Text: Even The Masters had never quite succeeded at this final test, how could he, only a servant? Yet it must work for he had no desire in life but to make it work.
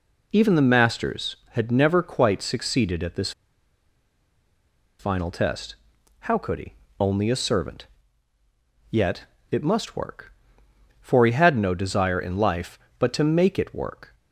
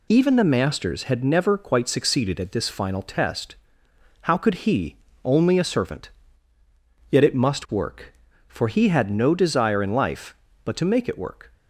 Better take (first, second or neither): second